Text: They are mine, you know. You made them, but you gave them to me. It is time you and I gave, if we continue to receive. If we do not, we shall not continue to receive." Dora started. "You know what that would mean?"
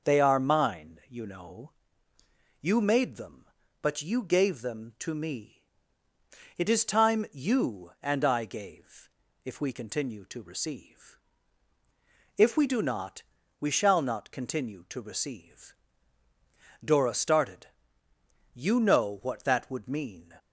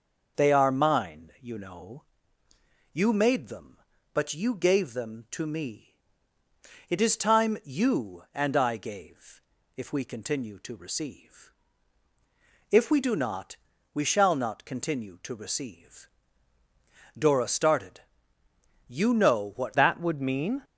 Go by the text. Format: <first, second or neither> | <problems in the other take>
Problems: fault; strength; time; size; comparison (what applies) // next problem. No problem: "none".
first | starts louder than the rest; noticeable; until 1.4 s; 6 dB; noticeable in the first // changes voice at "that"; from 19.7 s on; 0.9 s long